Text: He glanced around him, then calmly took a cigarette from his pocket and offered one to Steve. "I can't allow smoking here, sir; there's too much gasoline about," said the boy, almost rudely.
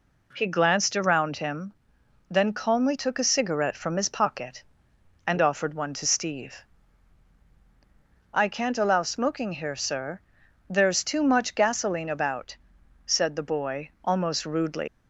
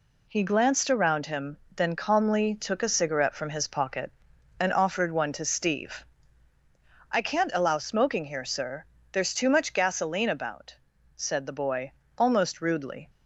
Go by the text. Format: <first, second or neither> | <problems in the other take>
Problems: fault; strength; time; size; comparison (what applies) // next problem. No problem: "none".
second | leaves "rudely" unfinished; at 14.8 s; 135 ms